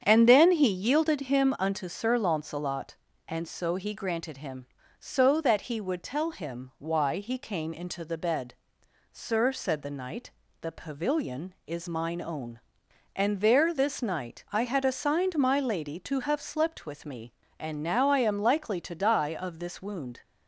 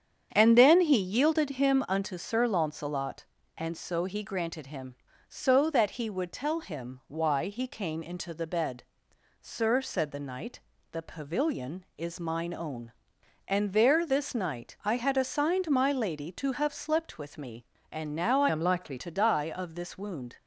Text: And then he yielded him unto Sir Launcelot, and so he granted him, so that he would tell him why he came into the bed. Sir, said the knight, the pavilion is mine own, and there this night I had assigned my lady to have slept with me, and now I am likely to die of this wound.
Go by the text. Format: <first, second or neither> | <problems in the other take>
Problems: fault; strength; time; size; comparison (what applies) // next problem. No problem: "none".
first | starts louder than the rest; strong; until 1.3 s; 8 dB; strong in the first // changes voice from "am" to "likely"; from 18.4 to 18.9 s; 0.5 s long